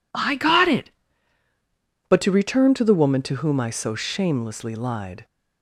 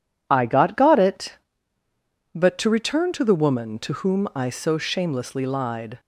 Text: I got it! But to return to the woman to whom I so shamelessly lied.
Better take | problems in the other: first | says "got" twice; at 0.7 s

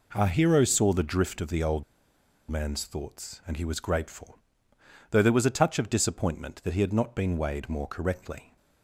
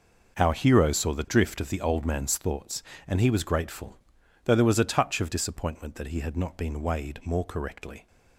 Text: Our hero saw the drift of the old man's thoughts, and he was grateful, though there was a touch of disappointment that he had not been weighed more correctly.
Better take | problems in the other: second | pauses between "old" and "man's"; noticeable; at 1.8 s; 0.66 s long

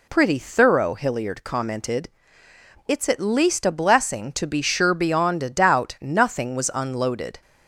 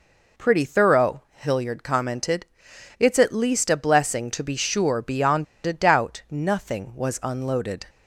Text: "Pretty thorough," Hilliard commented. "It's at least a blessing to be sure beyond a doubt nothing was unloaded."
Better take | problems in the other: first | pauses between "beyond" and "a"; slight; at 5.4 s; 0.21 s long

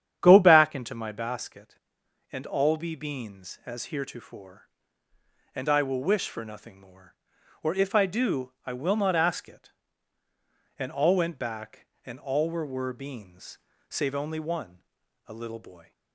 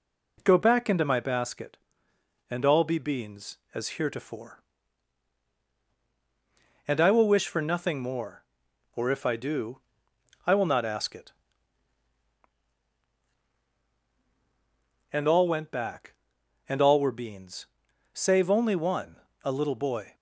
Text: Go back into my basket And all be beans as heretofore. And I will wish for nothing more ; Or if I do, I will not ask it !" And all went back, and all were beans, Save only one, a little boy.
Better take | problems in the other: second | starts louder than the rest; strong; until 1.2 s; 10 dB // says "were" twice; at 12.6 s

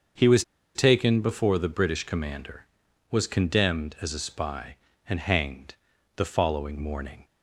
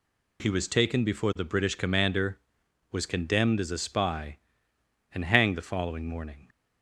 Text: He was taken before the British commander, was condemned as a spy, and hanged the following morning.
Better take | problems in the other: second | starts louder than the rest; until 1.4 s; 6.5 dB // pauses between "was" and "taken"; slight; at 0.4 s; 0.32 s long // pauses between "hanged" and "the"; at 5.7 s; 0.40 s long

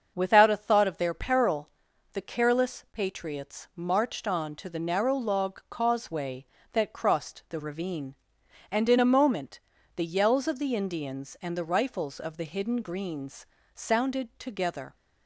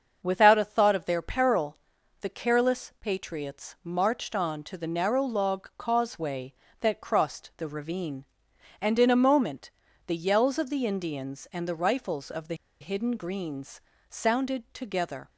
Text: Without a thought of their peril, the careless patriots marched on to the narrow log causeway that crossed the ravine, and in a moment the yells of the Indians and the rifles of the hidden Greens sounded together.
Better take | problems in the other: first | starts louder than the rest; until 1.2 s; 6.5 dB; also in the first // pauses between "moment" and "the"; slight; at 9.7 s; 0.34 s long; slight in the first // pauses between "the" and "hidden"; slight; at 12.5 s; 0.26 s long // pauses between "Greens" and "sounded"; slight; at 13.7 s; 0.28 s long; slight in the first

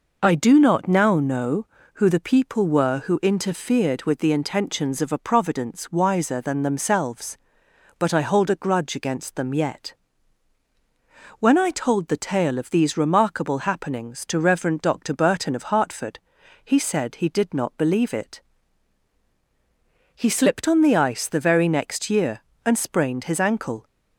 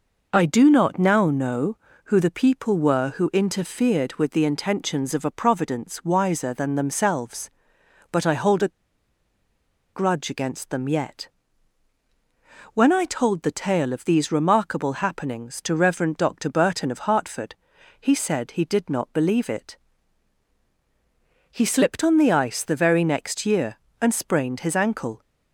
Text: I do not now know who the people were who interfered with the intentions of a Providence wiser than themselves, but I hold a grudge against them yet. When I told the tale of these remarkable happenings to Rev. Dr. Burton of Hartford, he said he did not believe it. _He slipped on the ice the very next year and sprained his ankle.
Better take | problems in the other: first | pauses between "a" and "grudge"; strong; at 8.6 s; 1.2 s long

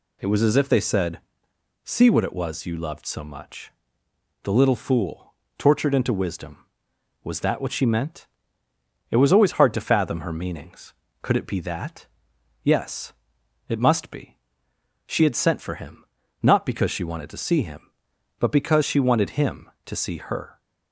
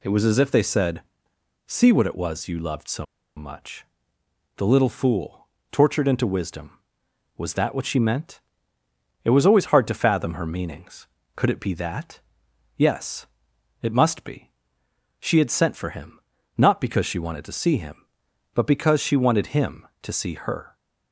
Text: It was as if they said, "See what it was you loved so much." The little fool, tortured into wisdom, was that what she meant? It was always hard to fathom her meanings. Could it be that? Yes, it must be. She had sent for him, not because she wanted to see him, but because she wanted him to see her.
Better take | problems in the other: first | pauses between "so" and "much"; slight; at 3.0 s; 0.32 s long

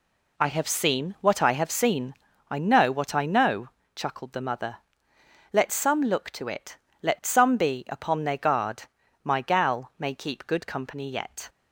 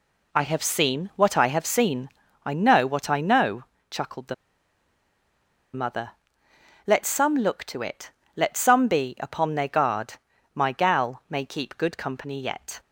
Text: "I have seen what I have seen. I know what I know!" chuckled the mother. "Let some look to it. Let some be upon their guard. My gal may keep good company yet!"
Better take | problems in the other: first | pauses between "the" and "mother"; strong; at 4.3 s; 1.4 s long

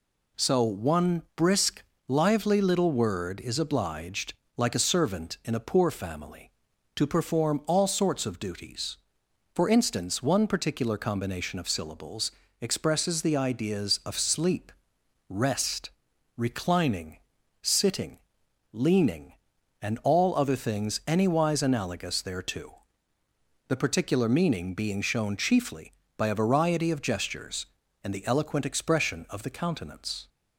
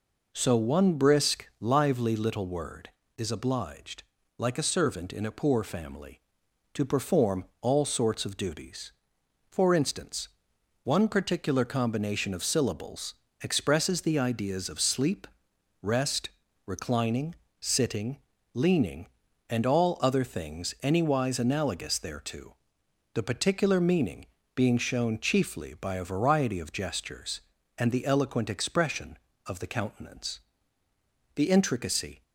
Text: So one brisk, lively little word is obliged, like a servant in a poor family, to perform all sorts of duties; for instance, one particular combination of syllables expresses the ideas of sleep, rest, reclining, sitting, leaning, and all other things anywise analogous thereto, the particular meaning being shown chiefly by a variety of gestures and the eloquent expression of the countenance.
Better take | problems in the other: first | pauses between "perform" and "all"; slight; at 7.4 s; 0.16 s long // pauses between "syllables" and "expresses"; slight; at 13.1 s; 0.28 s long; slight in the first // pauses between "meaning" and "being"; slight; at 24.2 s; 0.30 s long // goes on to say "The intricacy"; noticeable; from 31.3 s on; 0.88 s long

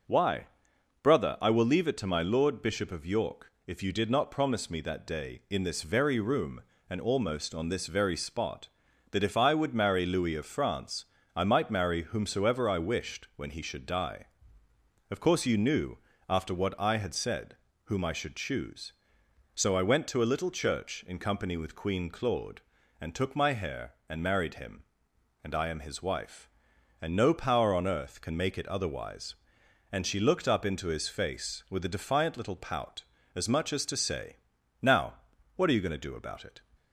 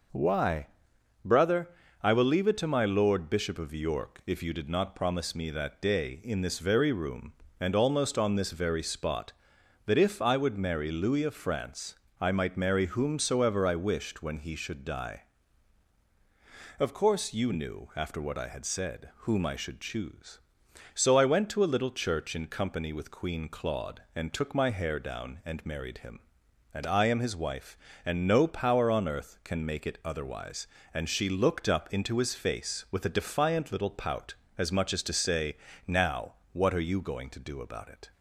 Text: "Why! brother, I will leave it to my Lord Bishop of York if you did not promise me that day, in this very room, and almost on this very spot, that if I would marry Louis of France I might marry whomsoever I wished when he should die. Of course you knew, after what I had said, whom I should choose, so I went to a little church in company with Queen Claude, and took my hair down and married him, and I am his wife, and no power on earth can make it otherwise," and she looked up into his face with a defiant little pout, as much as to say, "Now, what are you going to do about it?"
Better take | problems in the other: second | pauses between "France" and "I"; slight; at 11.0 s; 0.30 s long; slight in the second // skips "down"; at 24.0 s

